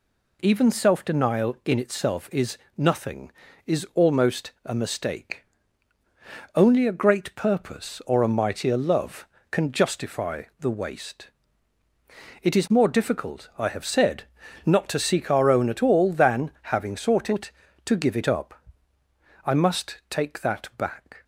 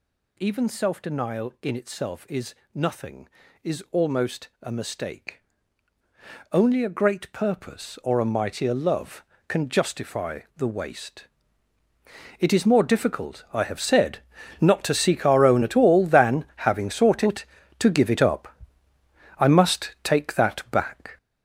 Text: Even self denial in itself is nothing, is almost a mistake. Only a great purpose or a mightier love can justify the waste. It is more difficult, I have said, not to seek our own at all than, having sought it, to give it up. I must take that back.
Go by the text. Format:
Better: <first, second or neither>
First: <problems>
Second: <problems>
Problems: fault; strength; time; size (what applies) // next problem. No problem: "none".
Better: first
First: pauses between "is" and "nothing"; slight; at 2.5 s; 0.20 s long // pauses between "justify" and "the"; slight; at 10.4 s; 0.16 s long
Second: gets louder; strong; throughout; 8.5 dB // pauses between "is" and "nothing"; slight; at 2.5 s; 0.20 s long // pauses between "justify" and "the"; slight; at 10.4 s; 0.16 s long